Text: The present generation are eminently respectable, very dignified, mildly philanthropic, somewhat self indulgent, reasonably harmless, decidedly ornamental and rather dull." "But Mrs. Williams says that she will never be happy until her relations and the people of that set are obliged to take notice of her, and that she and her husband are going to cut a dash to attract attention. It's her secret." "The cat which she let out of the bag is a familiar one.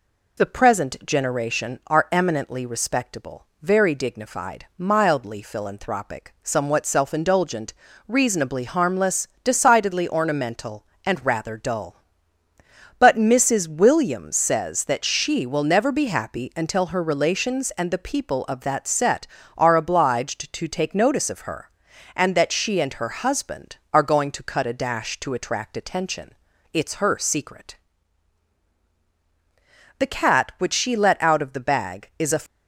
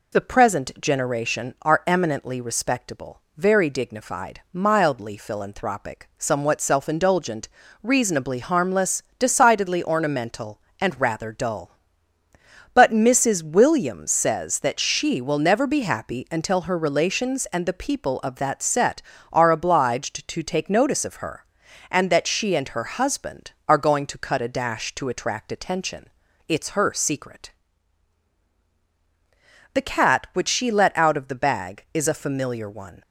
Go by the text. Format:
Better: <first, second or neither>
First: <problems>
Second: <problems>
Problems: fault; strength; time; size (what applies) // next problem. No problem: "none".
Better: second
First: stops before "familiar one"; at 32.4 s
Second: none